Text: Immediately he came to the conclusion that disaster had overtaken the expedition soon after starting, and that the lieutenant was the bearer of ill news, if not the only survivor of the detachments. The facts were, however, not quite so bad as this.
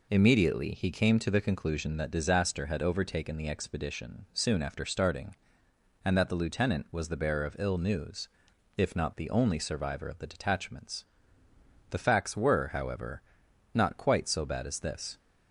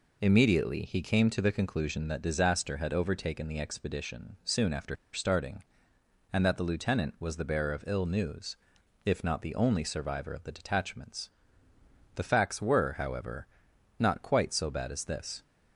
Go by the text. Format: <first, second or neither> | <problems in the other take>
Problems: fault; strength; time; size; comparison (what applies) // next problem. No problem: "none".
first | pauses between "after" and "starting"; slight; at 4.9 s; 0.17 s long